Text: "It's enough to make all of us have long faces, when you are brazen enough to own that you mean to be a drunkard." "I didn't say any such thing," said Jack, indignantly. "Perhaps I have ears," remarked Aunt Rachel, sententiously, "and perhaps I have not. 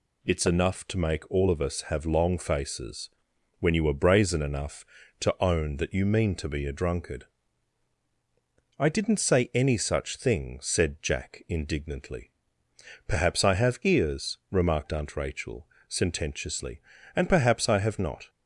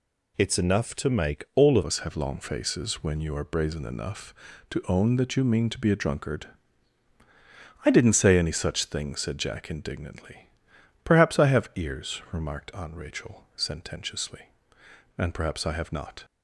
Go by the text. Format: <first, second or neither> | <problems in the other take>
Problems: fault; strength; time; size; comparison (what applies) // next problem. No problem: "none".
first | changes voice at "us"; from 1.8 s on; 14.4 s long